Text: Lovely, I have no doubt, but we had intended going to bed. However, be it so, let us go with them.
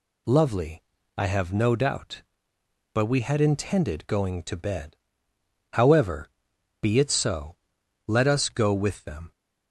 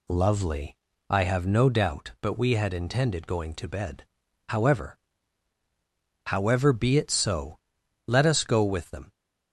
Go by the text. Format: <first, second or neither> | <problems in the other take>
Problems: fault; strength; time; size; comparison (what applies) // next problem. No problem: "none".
first | says "However" twice; at 6.2 s